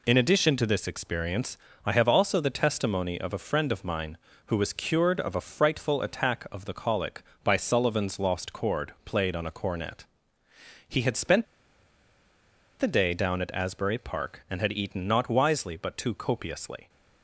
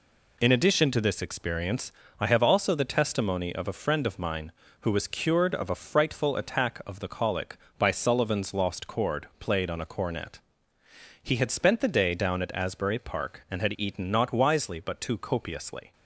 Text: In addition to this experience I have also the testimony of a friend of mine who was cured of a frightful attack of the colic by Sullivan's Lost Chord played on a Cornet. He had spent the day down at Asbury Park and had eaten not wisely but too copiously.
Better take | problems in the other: second | pauses between "experience" and "I"; slight; at 1.5 s; 0.28 s long; slight in the second // pauses between "spent" and "the"; strong; at 11.4 s; 1.3 s long

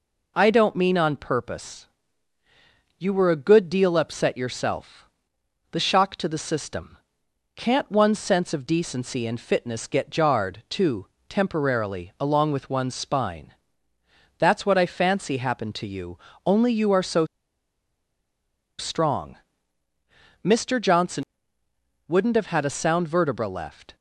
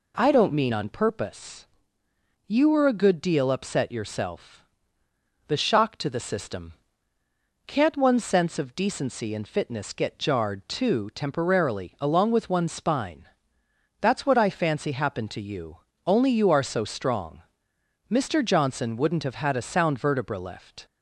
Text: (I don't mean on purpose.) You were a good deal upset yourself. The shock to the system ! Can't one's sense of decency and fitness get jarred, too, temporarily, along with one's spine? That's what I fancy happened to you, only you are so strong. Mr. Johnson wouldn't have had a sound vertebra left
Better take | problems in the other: second | pauses between "so" and "strong"; strong; at 17.2 s; 1.5 s long // pauses between "Johnson" and "wouldn't"; noticeable; at 21.2 s; 0.84 s long

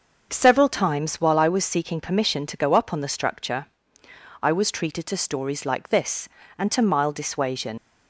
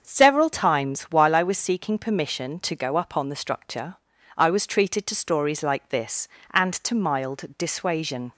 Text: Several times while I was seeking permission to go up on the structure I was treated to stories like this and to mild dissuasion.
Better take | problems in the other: second | starts louder than the rest; until 1.3 s; 6.5 dB; also in the second // pauses between "structure" and "I"; noticeable; at 3.6 s; 0.78 s long; also in the second // leaves "dissuasion" unfinished; at 7.7 s; 90 ms

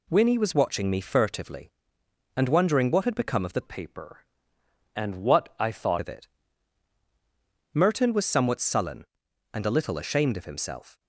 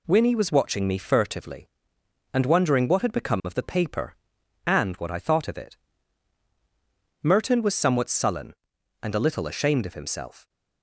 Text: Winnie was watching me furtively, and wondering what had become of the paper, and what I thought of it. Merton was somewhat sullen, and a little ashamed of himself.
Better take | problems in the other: second | changes voice from "paper" to "thought"; from 3.6 to 5.9 s; 2.3 s long

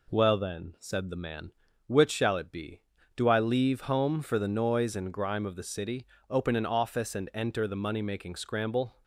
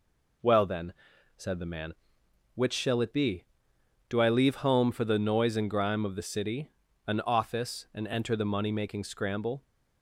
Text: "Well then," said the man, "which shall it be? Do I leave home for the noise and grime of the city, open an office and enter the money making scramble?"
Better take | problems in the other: first | skips "open"; at 6.8 s

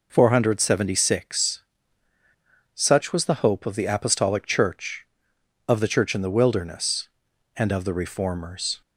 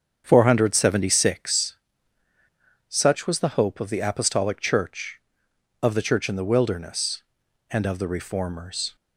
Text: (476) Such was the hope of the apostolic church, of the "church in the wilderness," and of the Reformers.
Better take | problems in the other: first | starts louder than the rest; strong; until 1.8 s; 7.5 dB

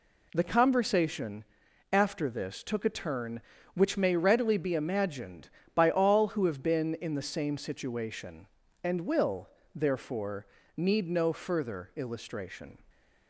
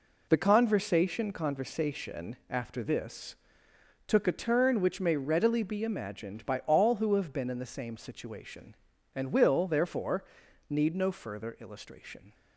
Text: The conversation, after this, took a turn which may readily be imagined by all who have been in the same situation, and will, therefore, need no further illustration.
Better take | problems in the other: first | says "conversation" twice; at 1.3 s

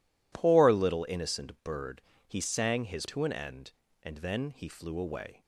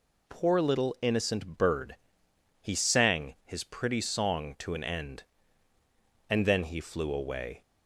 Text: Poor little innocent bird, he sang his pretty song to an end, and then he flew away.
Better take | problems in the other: second | skips "pretty song"; at 3.0 s

